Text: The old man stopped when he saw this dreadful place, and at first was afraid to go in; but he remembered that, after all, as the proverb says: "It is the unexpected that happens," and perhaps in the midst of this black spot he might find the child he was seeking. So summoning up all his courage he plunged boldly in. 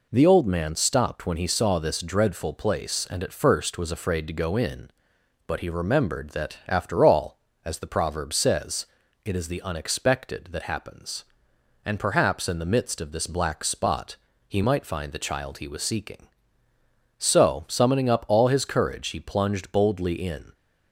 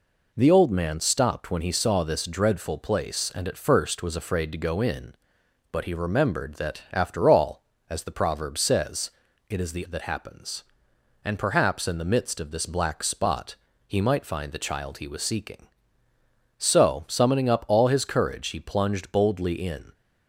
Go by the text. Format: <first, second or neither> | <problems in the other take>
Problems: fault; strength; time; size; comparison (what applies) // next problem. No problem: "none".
first | skips "unexpected"; at 9.8 s // pauses between "spot" and "he"; slight; at 13.5 s; 0.32 s long; slight in the first